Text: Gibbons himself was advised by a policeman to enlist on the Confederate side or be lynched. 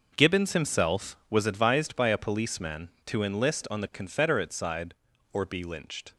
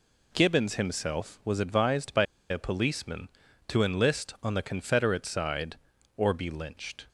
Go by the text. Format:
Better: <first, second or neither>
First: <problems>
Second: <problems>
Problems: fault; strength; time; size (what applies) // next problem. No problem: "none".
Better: first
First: none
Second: pauses between "by" and "a"; slight; at 2.2 s; 0.26 s long